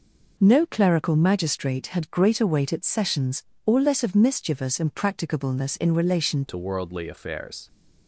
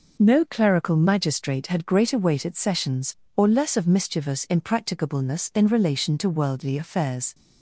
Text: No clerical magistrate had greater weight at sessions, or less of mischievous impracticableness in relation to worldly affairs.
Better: second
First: changes voice at "to"; from 6.4 s on; 1.2 s long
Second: none

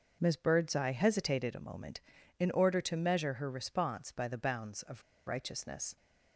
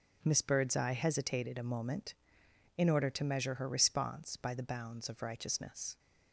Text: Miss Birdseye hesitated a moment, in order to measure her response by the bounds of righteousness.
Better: second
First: starts louder than the rest; noticeable; until 1.2 s; 6 dB // pauses between "of" and "righteousness"; slight; at 5.0 s; 0.24 s long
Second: starts louder than the rest; until 1.2 s; 6.5 dB

